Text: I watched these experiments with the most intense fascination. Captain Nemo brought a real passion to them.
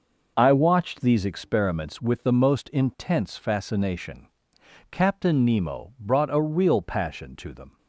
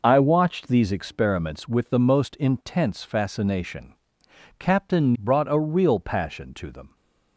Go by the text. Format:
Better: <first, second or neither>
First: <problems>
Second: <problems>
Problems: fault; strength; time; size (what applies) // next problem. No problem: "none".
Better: first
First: none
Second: skips "Nemo"; at 5.1 s